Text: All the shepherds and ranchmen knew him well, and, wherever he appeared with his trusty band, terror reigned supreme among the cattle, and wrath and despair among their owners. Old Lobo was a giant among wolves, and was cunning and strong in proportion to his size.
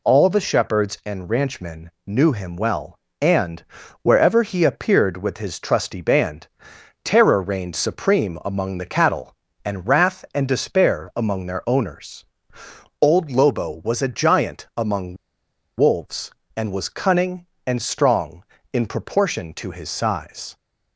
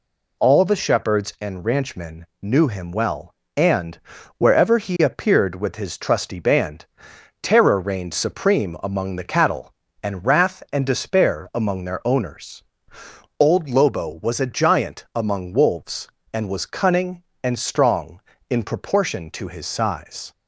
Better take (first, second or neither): second